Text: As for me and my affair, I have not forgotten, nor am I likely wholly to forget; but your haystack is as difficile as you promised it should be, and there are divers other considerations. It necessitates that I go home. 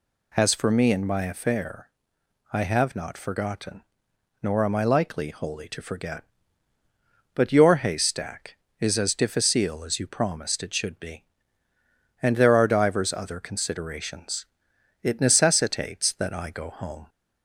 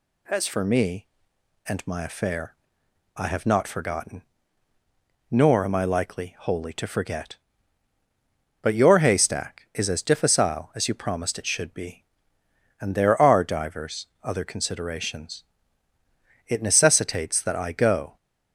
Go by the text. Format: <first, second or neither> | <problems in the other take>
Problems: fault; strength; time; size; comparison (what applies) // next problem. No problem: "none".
first | pauses between "divers" and "other"; slight; at 14.0 s; 0.16 s long // stops before "home"; at 18.1 s